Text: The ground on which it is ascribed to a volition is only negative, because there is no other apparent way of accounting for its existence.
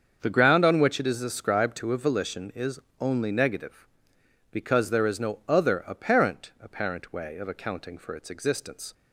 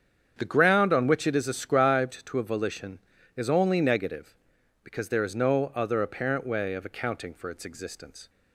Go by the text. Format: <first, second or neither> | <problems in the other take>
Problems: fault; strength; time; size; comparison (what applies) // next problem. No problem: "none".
second | starts louder than the rest; until 1.2 s; 7 dB; strong in the second // pauses between "is" and "only"; slight; at 2.7 s; 0.20 s long // says "apparent" twice; at 6.6 s